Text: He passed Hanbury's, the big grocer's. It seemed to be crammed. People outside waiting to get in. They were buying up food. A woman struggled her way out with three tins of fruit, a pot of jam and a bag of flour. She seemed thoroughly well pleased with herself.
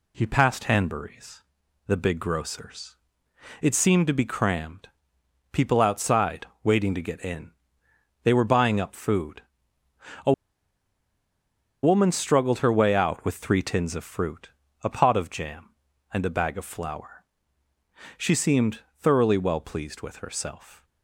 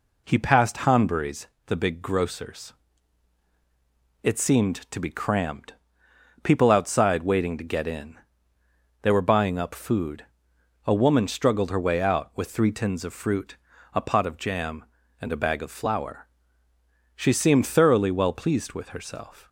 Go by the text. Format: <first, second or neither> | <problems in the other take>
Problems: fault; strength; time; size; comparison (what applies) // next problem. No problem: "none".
second | pauses between "outside" and "waiting"; slight; at 6.4 s; 0.18 s long // pauses between "A" and "woman"; strong; at 10.3 s; 1.5 s long // pauses between "seemed" and "thoroughly"; slight; at 18.8 s; 0.18 s long